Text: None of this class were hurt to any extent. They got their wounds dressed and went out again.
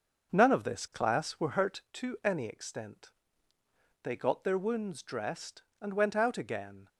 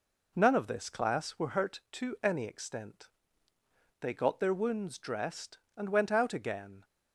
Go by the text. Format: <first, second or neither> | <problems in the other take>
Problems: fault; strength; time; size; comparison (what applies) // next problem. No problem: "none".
second | starts louder than the rest; noticeable; until 1.9 s; 6 dB